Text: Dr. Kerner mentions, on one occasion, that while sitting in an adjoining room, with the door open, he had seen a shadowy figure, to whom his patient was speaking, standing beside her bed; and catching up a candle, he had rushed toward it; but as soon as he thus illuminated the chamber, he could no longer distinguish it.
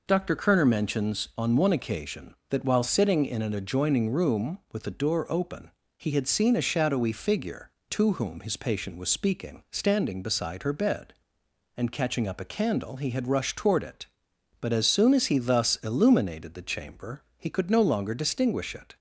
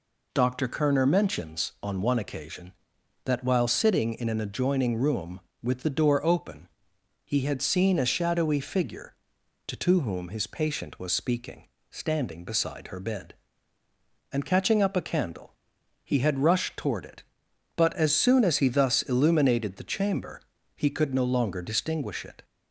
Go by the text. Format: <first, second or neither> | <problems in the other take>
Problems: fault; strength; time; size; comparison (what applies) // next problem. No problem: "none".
first | says "to" twice; at 9.7 s